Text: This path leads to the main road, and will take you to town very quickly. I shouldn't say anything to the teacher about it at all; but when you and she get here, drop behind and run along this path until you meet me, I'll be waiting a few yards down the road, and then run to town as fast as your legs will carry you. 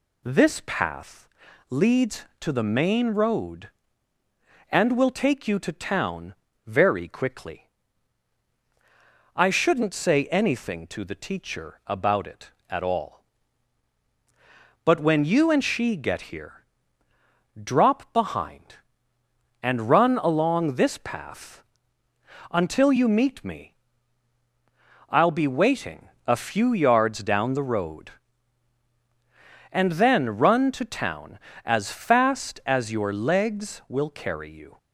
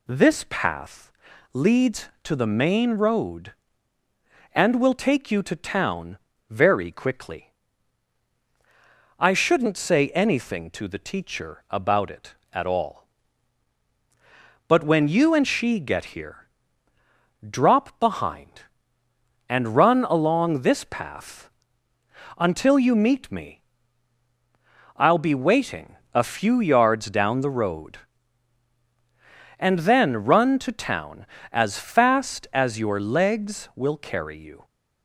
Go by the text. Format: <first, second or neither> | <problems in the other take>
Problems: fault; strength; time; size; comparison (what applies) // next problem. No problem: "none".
neither | pauses between "path" and "leads"; the same in both // pauses between "town" and "very"; slight; the same in both // pauses between "path" and "until"; noticeable; the same in both // pauses between "waiting" and "a"; slight; the same in both